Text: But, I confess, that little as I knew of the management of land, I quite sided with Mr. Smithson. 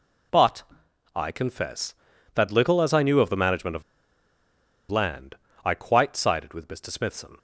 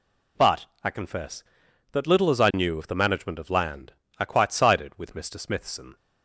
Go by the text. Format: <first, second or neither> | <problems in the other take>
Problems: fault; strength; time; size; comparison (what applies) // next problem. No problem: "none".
second | pauses between "of" and "land"; at 3.8 s; 1.0 s long